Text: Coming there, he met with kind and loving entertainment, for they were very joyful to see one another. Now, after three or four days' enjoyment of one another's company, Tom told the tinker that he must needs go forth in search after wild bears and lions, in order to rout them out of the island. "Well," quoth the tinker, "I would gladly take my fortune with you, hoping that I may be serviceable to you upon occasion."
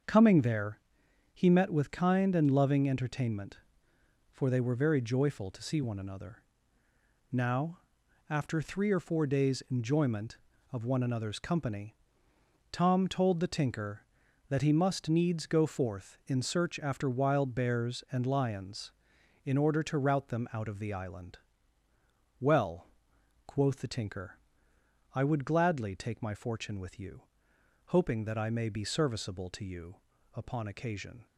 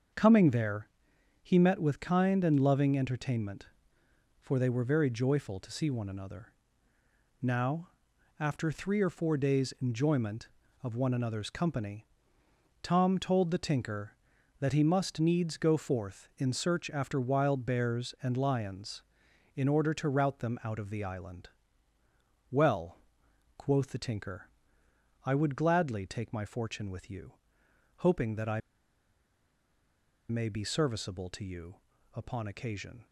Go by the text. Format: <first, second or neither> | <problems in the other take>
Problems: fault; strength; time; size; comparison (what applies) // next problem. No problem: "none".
first | starts louder than the rest; until 1.6 s; 6.5 dB; also in the first // pauses between "I" and "may"; strong; at 28.6 s; 1.6 s long // pauses between "you" and "upon"; at 31.7 s; 0.38 s long; also in the first